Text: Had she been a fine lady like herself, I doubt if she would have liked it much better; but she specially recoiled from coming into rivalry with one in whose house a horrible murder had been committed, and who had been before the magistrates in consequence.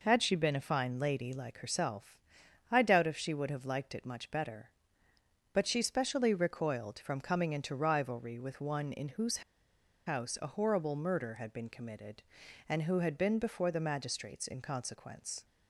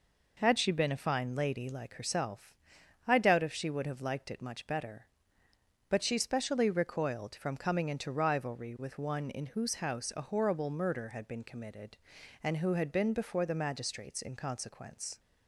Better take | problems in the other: second | pauses between "whose" and "house"; noticeable; at 9.4 s; 0.65 s long

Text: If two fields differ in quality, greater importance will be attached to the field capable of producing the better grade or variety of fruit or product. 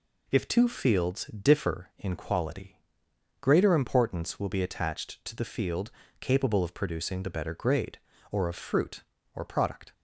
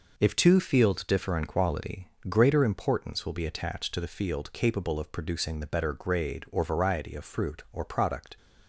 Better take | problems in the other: second | pauses between "field" and "capable"; slight; at 5.8 s; 0.30 s long // skips "variety"; at 8.4 s

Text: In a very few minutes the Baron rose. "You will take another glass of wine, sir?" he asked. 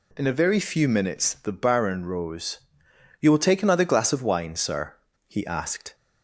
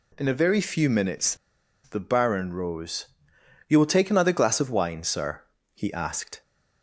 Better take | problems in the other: first | pauses between "minutes" and "the"; noticeable; at 1.3 s; 0.48 s long

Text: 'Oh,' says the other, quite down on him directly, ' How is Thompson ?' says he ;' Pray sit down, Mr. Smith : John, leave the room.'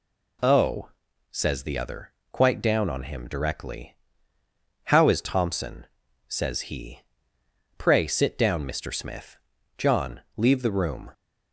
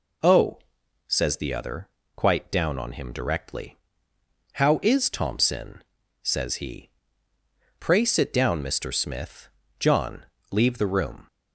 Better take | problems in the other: neither | none

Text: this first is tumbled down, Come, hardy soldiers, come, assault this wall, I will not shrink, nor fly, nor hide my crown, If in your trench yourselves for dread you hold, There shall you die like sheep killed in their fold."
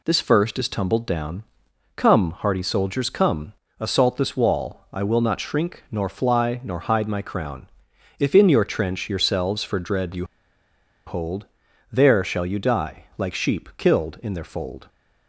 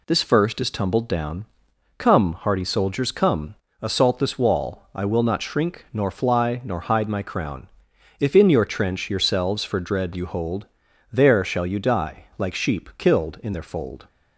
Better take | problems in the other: second | pauses between "you" and "hold"; noticeable; at 10.2 s; 0.82 s long

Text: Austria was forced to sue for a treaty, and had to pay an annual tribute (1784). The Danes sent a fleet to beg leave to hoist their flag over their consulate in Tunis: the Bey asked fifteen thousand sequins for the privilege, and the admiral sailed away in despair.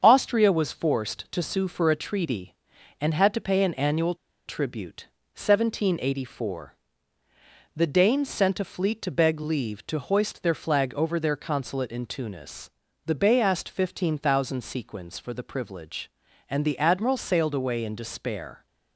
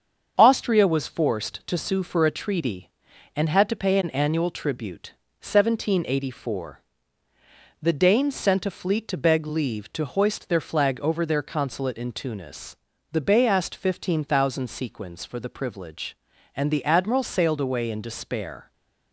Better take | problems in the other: second | starts louder than the rest; until 1.0 s; 7 dB; also in the second // pauses between "annual" and "tribute"; slight; at 4.1 s; 0.33 s long

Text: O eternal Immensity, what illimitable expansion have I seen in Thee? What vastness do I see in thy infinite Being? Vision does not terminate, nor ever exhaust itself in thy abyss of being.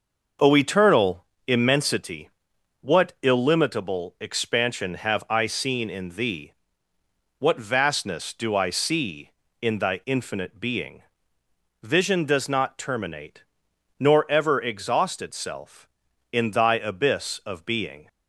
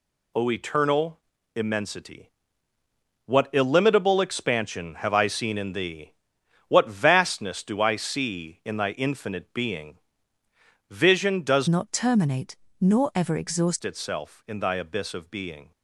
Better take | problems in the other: first | pauses between "eternal" and "Immensity"; slight; at 1.1 s; 0.36 s long; slight in the first // changes voice from "not" to "exhaust"; from 11.6 to 13.8 s; 2.2 s long

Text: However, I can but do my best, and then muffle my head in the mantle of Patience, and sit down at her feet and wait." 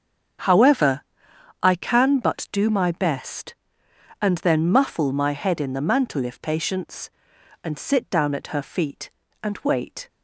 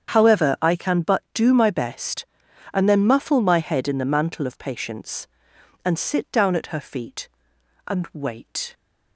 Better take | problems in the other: second | starts louder than the rest; strong; until 2.0 s; 7.5 dB; strong in the second // says "if" for "of"; at 6.2 s

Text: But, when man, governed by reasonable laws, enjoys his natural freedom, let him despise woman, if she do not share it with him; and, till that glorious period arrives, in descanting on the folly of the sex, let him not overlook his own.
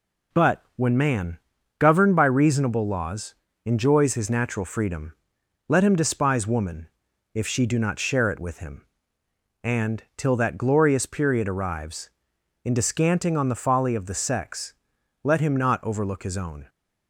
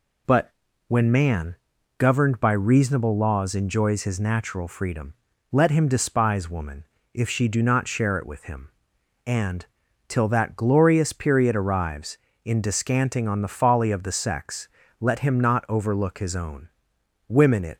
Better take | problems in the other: first | goes on to say "Women it"; from 17.2 s on; 0.50 s long

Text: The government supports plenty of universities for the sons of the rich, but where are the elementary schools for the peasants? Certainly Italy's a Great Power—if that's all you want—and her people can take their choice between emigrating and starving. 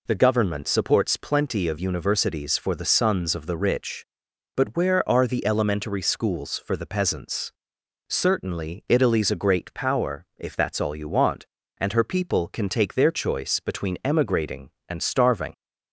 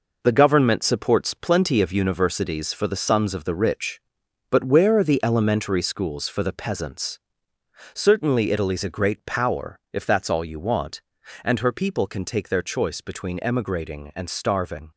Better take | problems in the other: first | gets quieter; throughout; 7 dB

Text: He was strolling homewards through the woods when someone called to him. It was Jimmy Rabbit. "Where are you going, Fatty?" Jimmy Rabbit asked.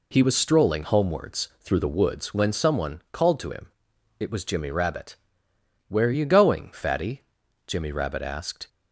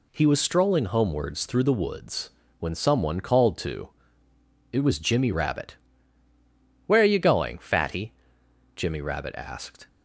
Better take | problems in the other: first | pauses between "woods" and "when"; slight; at 2.3 s; 0.28 s long // skips "him"; at 4.3 s

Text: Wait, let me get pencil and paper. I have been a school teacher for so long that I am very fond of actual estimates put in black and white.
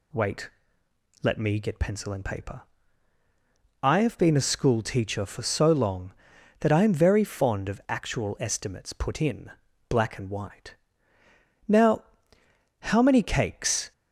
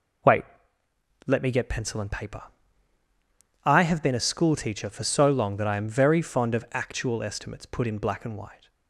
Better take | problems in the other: second | pauses between "in" and "black"; at 9.4 s; 0.39 s long // goes on to say "Now how many cakes"; strong; from 11.6 s on; 2.2 s long

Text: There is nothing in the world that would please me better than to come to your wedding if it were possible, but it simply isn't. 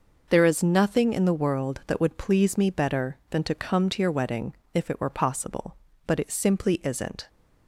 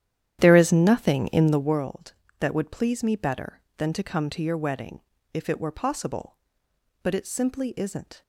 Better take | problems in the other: first | starts louder than the rest; strong; until 1.8 s; 10.5 dB // pauses between "wedding" and "if"; slight; at 5.0 s; 0.32 s long; slight in the first

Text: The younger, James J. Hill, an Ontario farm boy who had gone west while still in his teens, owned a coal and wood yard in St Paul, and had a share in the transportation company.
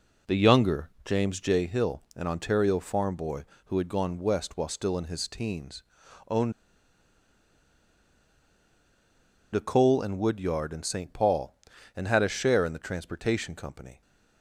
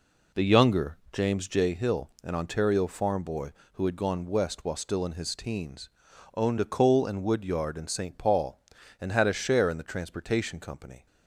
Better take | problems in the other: second | pauses between "owned" and "a"; strong; at 6.5 s; 3.0 s long

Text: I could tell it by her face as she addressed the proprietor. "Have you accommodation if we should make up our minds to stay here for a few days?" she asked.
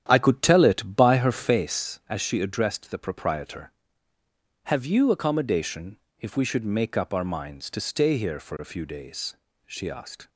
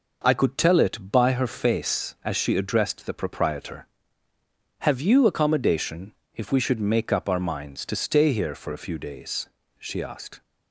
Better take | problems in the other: second | starts louder than the rest; strong; until 1.8 s; 10 dB // pauses between "accommodation" and "if"; slight; at 5.9 s; 0.24 s long; slight in the second

